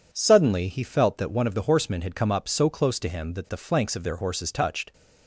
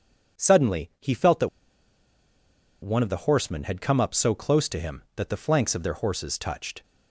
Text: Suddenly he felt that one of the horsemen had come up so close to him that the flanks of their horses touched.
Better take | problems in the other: first | pauses between "that" and "one"; strong; at 1.4 s; 1.3 s long

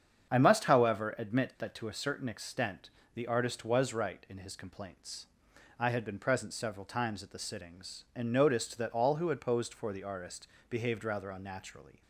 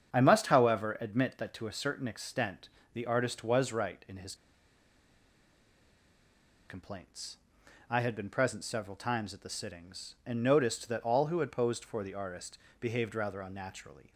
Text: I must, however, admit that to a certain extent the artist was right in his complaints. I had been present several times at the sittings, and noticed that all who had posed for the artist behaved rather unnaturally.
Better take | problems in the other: first | starts louder than the rest; strong; until 1.1 s; 7.5 dB; strong in the first // pauses between "extent" and "the"; slight; at 2.6 s; 0.24 s long; slight in the first // pauses between "his" and "complaints"; strong; at 4.3 s; 2.3 s long // pauses between "artist" and "behaved"; slight; at 12.5 s; 0.22 s long; slight in the first

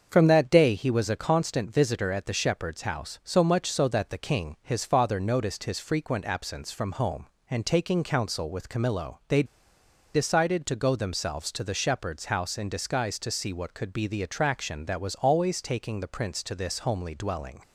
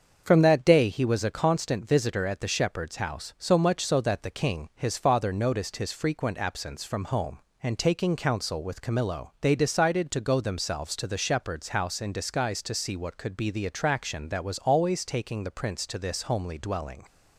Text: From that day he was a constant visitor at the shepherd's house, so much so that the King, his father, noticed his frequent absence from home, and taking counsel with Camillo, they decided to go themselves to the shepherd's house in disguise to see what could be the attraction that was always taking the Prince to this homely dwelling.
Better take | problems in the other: second | starts louder than the rest; until 1.1 s; 6.5 dB; also in the second // pauses between "they" and "decided"; noticeable; at 9.4 s; 0.70 s long

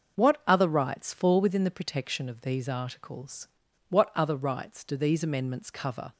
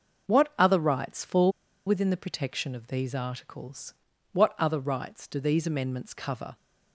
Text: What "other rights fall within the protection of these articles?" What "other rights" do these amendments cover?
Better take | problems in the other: first | pauses between "fall" and "within"; at 1.5 s; 0.36 s long

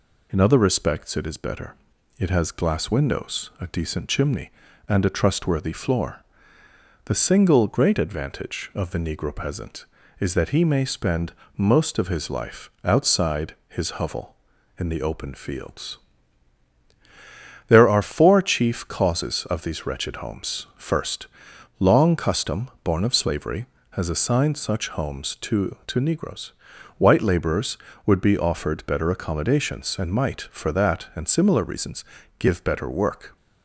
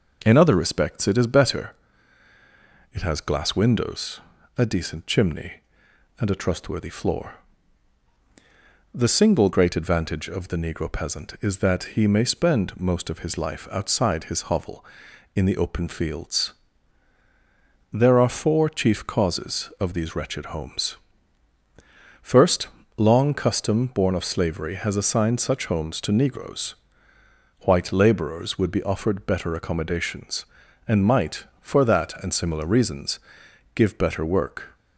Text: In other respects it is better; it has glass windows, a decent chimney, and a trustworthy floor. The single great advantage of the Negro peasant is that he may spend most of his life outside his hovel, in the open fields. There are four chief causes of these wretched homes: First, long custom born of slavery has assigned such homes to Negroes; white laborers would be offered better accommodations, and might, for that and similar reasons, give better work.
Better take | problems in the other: second | pauses between "spend" and "most"; slight; at 11.3 s; 0.24 s long // says "to" twice; at 25.8 s

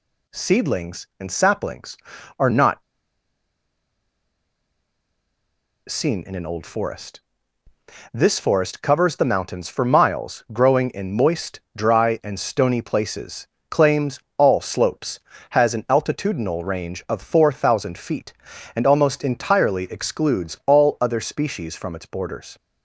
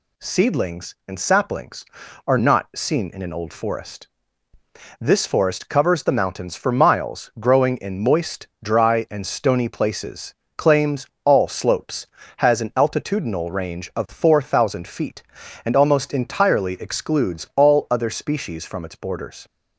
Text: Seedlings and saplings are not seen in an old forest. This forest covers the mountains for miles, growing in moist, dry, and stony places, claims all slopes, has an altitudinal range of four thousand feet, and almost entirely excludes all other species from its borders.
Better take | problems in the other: second | pauses between "not" and "seen"; strong; at 2.8 s; 3.0 s long // pauses between "claims" and "all"; slight; at 14.1 s; 0.20 s long; slight in the second

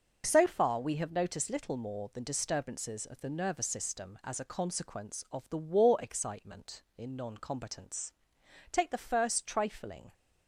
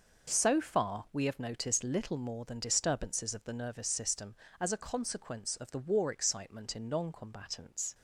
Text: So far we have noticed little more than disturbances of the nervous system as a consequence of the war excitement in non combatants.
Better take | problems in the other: second | goes on to say "Take the first trifling"; from 8.7 s on; 1.4 s long

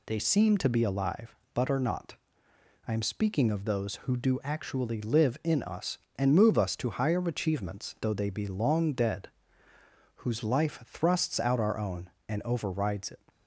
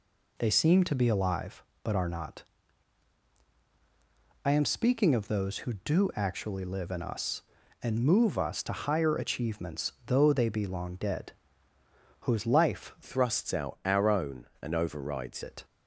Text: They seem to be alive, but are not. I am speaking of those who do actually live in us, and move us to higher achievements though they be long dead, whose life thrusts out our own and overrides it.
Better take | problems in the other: first | changes voice from "thrusts" to "overrides"; from 13.0 to 15.4 s; 2.4 s long

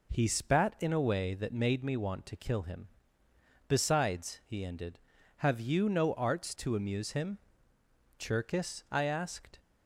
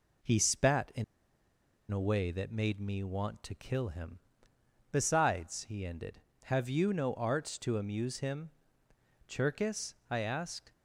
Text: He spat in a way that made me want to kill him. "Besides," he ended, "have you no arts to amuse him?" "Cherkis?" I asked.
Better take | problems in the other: first | pauses between "in" and "a"; noticeable; at 1.0 s; 0.87 s long

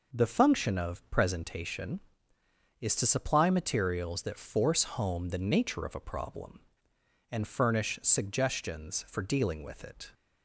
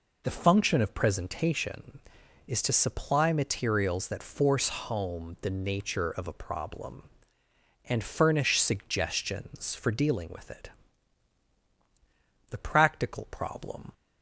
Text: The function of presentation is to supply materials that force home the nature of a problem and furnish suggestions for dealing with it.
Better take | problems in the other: first | goes on to say "The practical problem"; from 12.4 s on; 1.4 s long

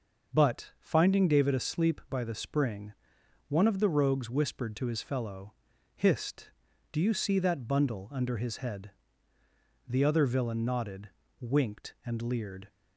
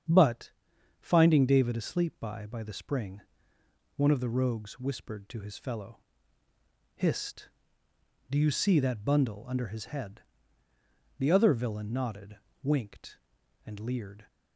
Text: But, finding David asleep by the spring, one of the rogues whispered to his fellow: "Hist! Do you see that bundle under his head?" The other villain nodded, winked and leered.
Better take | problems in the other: first | starts louder than the rest; strong; until 1.5 s; 8 dB; noticeable in the first // says "by" twice; at 2.4 s

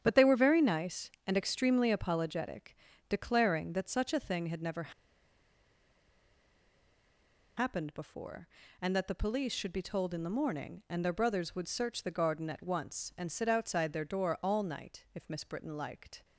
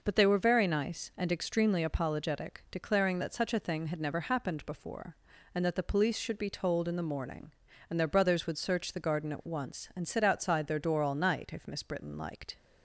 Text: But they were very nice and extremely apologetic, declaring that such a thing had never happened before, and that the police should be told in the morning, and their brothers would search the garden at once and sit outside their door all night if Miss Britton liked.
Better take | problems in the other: second | starts louder than the rest; strong; until 1.0 s; 9 dB // pauses between "never" and "happened"; strong; at 4.9 s; 2.6 s long

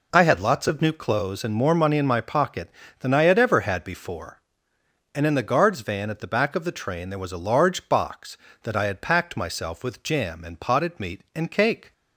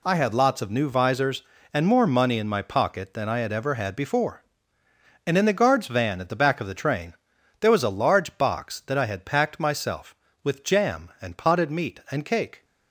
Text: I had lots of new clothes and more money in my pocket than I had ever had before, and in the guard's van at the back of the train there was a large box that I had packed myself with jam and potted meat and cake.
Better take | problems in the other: first | says "visors" for "clothes"; at 0.8 s // pauses between "train" and "there"; noticeable; at 7.1 s; 0.46 s long

